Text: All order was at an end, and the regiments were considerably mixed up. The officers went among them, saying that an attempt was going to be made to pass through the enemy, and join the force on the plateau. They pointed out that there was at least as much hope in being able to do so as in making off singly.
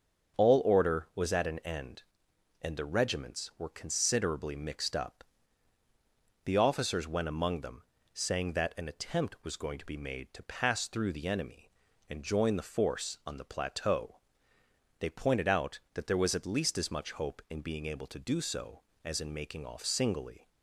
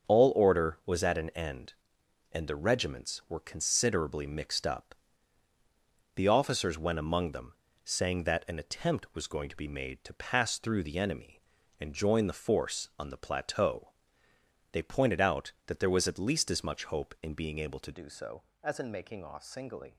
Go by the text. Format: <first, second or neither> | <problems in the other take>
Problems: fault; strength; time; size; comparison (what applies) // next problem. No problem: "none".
first | starts louder than the rest; until 1.1 s; 6.5 dB; also in the first // changes voice at "do"; from 17.9 s on; 2.0 s long